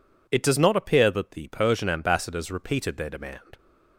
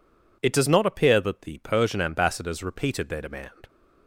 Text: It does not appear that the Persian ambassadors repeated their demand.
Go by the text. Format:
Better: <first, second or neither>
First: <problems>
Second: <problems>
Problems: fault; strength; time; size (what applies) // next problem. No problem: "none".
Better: neither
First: none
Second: none